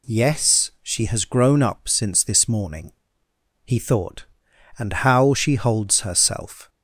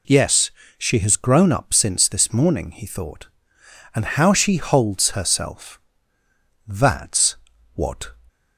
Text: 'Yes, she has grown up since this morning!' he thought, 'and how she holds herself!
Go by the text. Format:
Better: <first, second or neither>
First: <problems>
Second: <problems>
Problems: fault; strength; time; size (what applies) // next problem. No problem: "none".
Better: first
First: none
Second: goes on to say "That's what"; from 6.6 s on; 1.4 s long